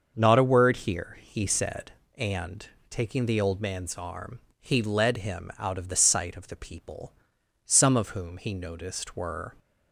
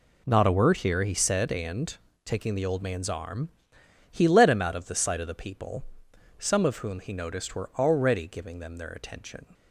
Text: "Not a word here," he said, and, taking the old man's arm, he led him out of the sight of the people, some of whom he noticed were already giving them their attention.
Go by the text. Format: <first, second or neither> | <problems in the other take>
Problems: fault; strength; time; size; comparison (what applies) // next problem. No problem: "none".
second | starts louder than the rest; until 1.1 s; 6.5 dB // stops before "already giving them their attention"; at 9.5 s